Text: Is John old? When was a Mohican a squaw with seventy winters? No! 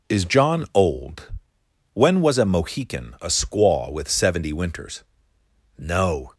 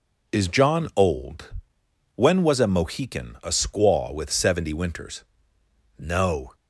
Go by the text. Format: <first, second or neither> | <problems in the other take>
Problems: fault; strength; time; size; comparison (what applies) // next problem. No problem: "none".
neither | none